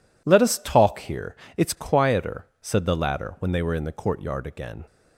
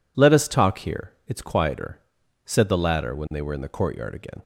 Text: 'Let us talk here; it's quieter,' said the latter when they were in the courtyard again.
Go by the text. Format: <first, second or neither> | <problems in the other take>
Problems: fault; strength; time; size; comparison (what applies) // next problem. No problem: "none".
neither | none